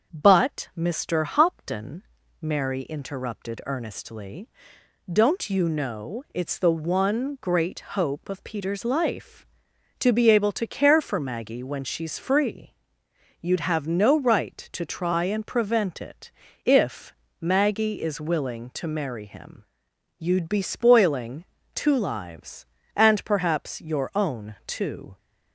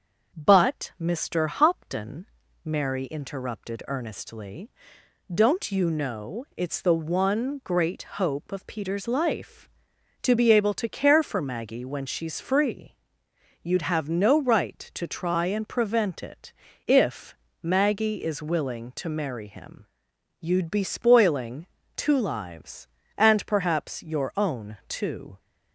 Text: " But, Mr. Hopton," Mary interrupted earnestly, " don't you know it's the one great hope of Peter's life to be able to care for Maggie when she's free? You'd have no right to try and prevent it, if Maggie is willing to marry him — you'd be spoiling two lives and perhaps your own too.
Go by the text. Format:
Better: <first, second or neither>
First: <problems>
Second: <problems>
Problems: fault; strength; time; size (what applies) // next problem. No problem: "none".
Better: neither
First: starts louder than the rest; until 1.1 s; 6.5 dB // pauses between "if" and "Maggie"; slight; at 17.1 s; 0.26 s long // pauses between "spoiling" and "two"; slight; at 21.4 s; 0.30 s long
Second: starts louder than the rest; until 1.3 s; 6.5 dB // pauses between "if" and "Maggie"; slight; at 17.3 s; 0.26 s long // pauses between "spoiling" and "two"; slight; at 21.6 s; 0.30 s long